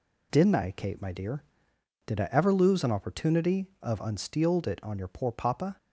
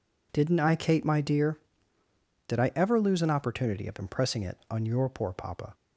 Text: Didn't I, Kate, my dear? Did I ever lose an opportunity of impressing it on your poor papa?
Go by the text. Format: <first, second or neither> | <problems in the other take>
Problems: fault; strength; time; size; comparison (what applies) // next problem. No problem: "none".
second | says "unsteeled" for "impressing"; at 3.9 s